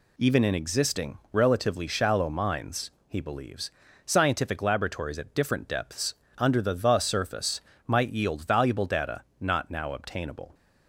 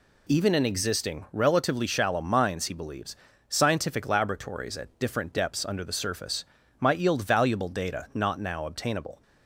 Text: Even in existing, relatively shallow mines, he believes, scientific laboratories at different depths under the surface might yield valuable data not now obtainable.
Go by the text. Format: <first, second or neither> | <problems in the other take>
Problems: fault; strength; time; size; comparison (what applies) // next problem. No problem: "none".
second | pauses between "depths" and "under"; slight; at 6.1 s; 0.24 s long // says "the" twice; at 6.7 s // pauses between "surface" and "might"; slight; at 7.5 s; 0.26 s long; slight in the second // pauses between "data" and "not"; slight; at 9.2 s; 0.18 s long